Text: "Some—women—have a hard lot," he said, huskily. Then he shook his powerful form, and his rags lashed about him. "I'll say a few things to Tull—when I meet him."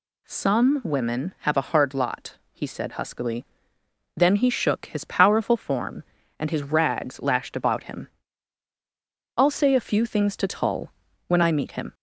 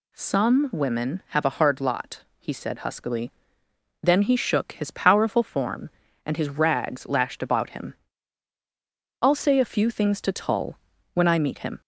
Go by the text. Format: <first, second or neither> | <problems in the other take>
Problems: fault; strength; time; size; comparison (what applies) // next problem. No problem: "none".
neither | none